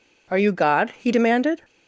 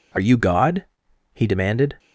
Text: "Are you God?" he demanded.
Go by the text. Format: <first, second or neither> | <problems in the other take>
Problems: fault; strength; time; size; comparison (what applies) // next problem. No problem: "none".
first | changes voice at "you"; from 0.1 s on; 1.8 s long